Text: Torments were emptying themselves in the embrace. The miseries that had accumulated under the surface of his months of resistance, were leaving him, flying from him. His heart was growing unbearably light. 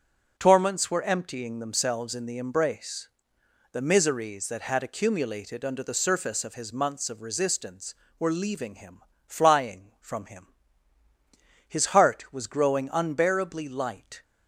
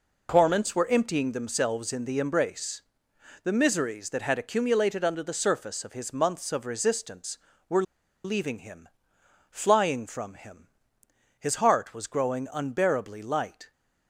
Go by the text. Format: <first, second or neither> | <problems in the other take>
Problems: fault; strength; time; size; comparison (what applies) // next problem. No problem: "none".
first | pauses between "were" and "leaving"; at 7.8 s; 0.42 s long